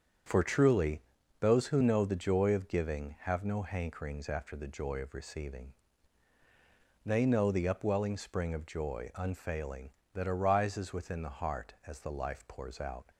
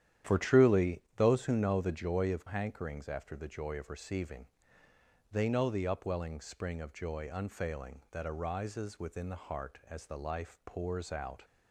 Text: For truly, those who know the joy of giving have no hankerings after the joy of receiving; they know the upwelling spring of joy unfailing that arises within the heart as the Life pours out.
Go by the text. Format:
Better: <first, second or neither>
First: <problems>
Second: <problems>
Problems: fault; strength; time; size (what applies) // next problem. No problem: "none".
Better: first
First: starts louder than the rest; strong; until 1.6 s; 7.5 dB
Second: starts louder than the rest; strong; until 1.4 s; 10.5 dB // skips "giving have no"; at 2.4 s